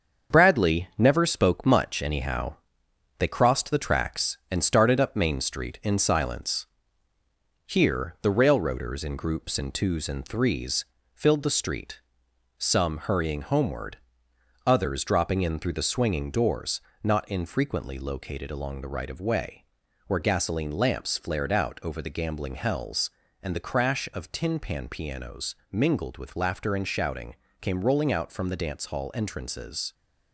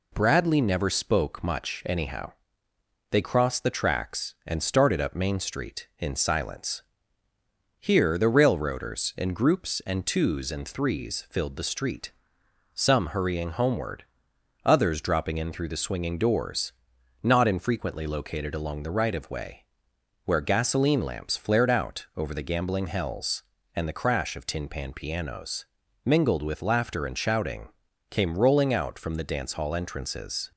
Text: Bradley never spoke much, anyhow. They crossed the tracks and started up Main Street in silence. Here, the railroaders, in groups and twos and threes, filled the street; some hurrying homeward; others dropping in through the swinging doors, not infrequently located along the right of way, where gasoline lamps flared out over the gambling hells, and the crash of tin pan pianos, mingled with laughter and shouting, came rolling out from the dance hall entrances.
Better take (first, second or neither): second